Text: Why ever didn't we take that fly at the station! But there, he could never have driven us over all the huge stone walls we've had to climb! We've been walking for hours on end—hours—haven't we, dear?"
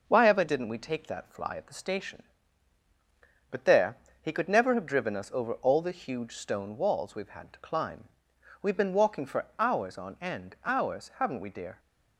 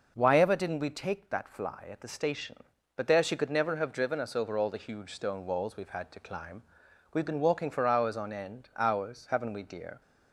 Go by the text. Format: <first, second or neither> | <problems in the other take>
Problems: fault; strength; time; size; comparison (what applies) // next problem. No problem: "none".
first | says "she" for "he"; at 3.2 s